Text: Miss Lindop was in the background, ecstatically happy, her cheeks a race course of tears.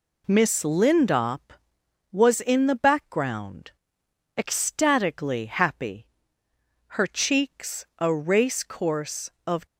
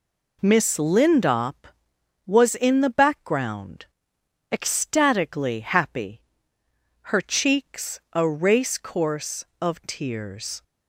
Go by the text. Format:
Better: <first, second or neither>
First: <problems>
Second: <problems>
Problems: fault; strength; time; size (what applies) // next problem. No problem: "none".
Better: second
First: stops before "tears"; at 9.6 s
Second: none